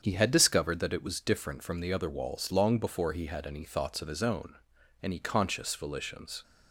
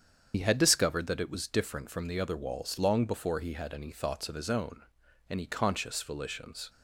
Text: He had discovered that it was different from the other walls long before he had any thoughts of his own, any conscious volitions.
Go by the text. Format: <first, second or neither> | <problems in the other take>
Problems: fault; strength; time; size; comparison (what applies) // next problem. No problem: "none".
first | loses the start of "He"; at 0.3 s; 50 ms // starts louder than the rest; strong; until 1.3 s; 7.5 dB; strong in the first